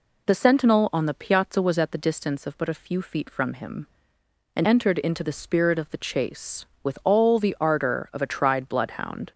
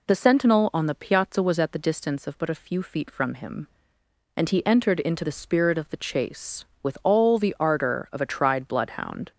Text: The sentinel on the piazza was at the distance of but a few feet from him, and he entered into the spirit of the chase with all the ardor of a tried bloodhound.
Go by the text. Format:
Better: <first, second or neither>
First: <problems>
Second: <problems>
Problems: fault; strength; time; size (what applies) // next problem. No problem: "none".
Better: second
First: skips "he"; at 4.6 s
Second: none